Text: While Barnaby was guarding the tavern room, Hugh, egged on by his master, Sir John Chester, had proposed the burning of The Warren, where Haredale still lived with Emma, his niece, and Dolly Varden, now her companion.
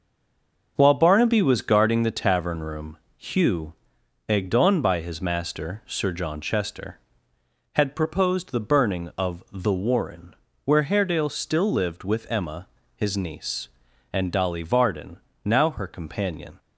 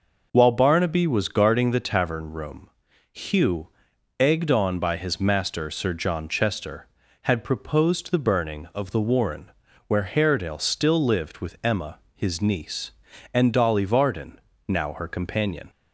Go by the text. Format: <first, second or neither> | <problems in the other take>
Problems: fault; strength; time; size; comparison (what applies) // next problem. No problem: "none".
second | stays silent before the first word; slight; until 0.7 s; 0.7 s long